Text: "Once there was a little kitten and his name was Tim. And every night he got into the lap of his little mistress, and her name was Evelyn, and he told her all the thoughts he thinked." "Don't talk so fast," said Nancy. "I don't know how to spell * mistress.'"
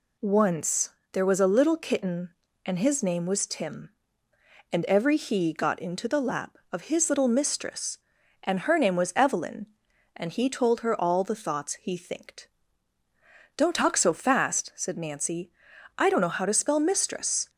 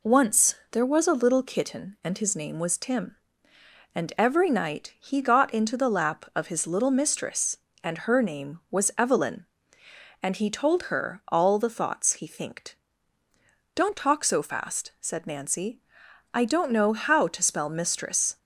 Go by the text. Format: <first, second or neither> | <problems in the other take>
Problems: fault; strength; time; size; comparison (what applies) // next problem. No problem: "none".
second | pauses between "Once" and "there"; slight; at 0.8 s; 0.22 s long; slight in the second // skips "night"; at 5.1 s